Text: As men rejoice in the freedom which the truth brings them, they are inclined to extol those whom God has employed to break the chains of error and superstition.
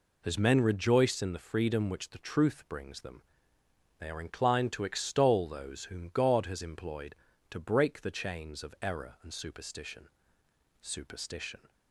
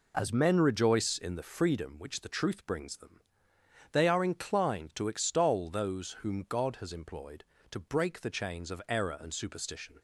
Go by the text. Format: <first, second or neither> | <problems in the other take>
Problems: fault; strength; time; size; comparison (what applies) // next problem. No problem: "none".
second | says "superstition" twice; at 10.8 s